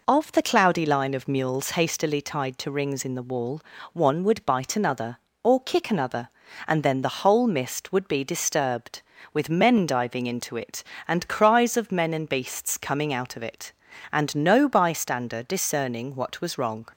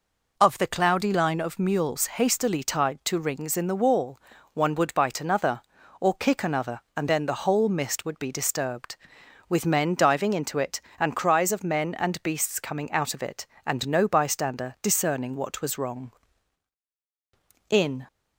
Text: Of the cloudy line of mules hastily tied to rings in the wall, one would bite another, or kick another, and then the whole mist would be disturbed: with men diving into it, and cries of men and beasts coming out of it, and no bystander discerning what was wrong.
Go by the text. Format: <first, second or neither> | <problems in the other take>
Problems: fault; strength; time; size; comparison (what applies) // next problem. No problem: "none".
first | goes on to say "In"; slight; from 17.6 s on; 0.36 s long